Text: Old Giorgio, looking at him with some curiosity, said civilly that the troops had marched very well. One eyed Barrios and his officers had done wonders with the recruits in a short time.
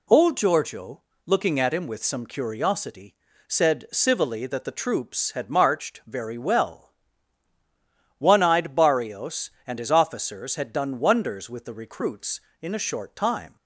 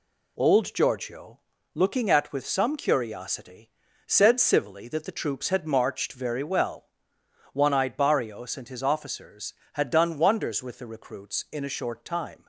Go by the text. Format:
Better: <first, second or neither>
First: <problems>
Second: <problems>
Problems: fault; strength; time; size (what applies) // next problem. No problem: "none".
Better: first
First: none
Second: skips "him"; at 2.3 s